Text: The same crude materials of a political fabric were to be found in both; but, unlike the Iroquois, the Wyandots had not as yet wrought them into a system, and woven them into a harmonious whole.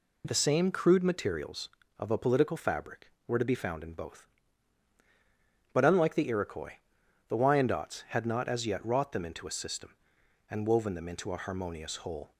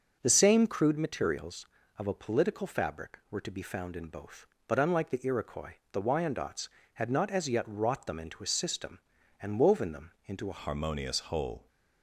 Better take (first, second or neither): first